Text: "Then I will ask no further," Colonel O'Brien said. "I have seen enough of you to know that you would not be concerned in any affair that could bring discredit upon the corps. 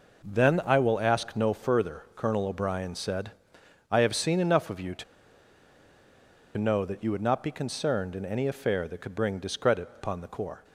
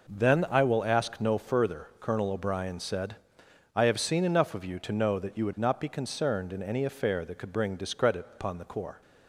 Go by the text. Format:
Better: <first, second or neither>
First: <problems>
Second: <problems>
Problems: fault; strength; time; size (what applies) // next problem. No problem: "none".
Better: second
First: pauses between "to" and "know"; strong; at 5.0 s; 1.5 s long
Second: none